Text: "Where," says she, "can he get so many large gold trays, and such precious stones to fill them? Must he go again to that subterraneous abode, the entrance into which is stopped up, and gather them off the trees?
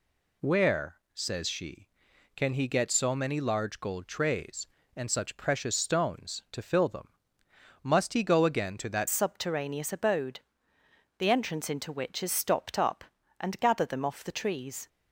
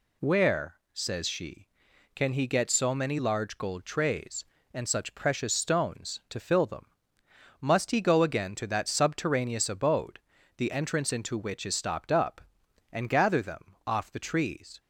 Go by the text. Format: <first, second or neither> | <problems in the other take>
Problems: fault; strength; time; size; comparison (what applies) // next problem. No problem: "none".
second | changes voice at "subterraneous"; from 9.0 s on; 5.8 s long